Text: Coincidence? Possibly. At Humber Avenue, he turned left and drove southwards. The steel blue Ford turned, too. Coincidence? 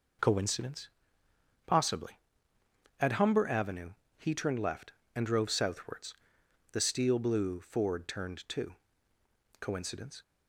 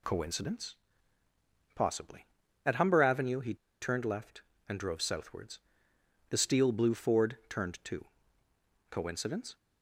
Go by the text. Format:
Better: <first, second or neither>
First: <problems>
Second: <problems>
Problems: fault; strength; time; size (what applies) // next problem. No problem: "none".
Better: first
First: none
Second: pauses between "he" and "turned"; slight; at 3.5 s; 0.26 s long